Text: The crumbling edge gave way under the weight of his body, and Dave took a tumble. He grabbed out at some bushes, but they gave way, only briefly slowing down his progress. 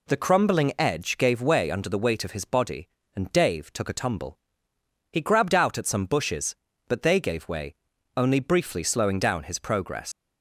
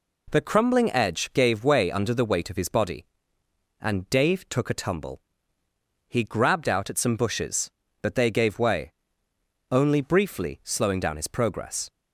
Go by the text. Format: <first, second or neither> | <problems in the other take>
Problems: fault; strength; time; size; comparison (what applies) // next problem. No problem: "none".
second | leaves "progress" unfinished; at 10.1 s; 120 ms